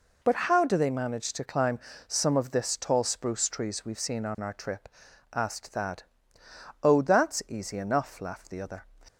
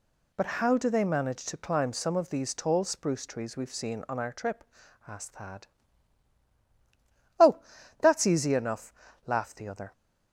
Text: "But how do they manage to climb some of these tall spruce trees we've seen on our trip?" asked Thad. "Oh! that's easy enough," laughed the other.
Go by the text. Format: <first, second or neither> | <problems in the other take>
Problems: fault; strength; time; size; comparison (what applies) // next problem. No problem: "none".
second | pauses between "climb" and "some"; slight; at 1.7 s; 0.26 s long // says "this" for "these"; at 2.5 s